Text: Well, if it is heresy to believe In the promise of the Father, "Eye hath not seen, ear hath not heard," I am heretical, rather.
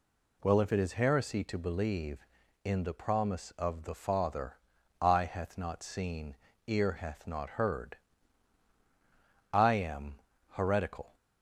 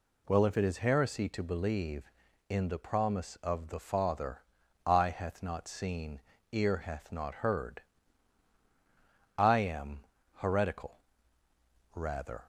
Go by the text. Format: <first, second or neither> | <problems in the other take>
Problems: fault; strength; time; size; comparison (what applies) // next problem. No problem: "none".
second | pauses between "am" and "heretical"; slight; at 10.1 s; 0.30 s long; slight in the second // stops before "rather"; at 11.1 s